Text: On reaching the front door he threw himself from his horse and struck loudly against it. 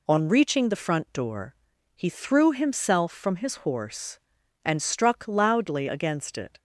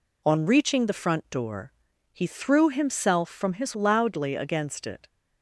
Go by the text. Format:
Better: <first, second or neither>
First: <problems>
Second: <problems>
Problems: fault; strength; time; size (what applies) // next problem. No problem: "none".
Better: first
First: pauses between "door" and "he"; at 1.5 s; 0.40 s long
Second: pauses between "door" and "he"; at 1.7 s; 0.40 s long // skips "horse and struck"; at 3.7 s